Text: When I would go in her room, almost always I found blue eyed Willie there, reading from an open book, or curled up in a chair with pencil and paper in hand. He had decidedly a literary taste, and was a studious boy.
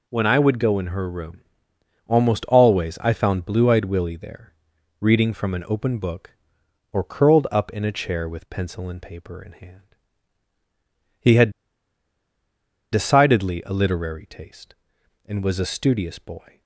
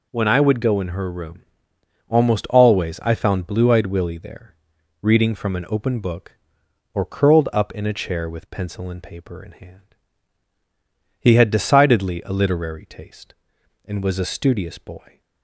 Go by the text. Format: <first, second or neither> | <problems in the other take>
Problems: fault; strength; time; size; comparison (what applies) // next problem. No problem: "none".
second | pauses between "had" and "decidedly"; strong; at 11.4 s; 1.4 s long